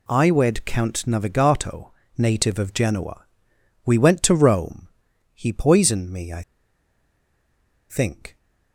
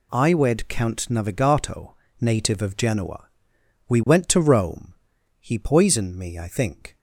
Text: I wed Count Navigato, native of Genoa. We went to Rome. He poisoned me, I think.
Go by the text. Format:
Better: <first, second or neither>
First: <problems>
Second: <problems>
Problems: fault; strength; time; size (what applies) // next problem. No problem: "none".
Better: second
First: pauses between "I" and "think"; strong; at 6.4 s; 1.4 s long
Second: none